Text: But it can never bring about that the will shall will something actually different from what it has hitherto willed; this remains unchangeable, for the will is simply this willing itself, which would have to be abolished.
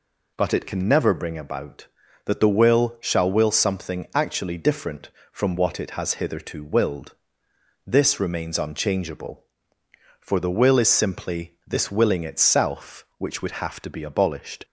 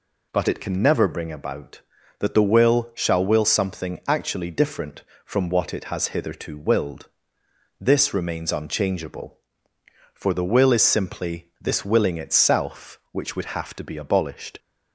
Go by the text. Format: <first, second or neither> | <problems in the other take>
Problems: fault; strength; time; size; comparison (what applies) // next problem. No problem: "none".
neither | none